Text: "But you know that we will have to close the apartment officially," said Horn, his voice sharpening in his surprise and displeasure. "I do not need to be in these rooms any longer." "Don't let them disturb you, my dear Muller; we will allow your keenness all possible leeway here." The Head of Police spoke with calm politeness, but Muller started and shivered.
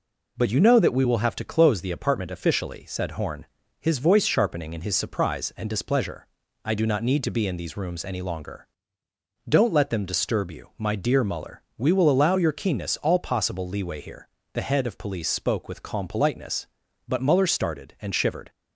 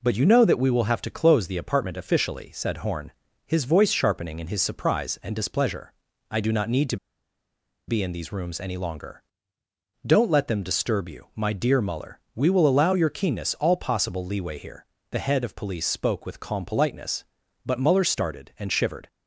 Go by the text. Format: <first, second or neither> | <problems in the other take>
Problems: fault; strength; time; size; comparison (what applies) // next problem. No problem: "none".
first | pauses between "to" and "be"; noticeable; at 6.9 s; 0.92 s long